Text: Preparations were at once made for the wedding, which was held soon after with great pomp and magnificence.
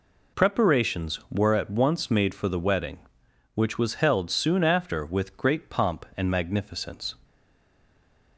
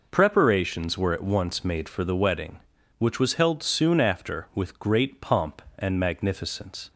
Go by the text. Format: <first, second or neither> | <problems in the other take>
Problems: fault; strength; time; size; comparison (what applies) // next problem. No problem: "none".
second | stays silent after the last word; from 7.2 s on; 1.1 s long